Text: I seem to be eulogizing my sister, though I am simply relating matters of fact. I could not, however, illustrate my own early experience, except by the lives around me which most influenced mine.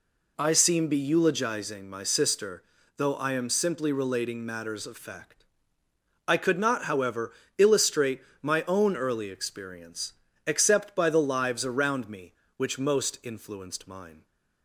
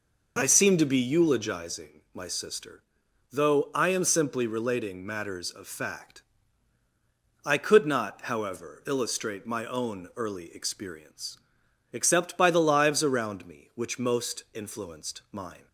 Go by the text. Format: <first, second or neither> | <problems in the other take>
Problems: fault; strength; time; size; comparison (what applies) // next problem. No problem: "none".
second | skips "to"; at 0.8 s // pauses between "illustrate" and "my"; slight; at 8.2 s; 0.20 s long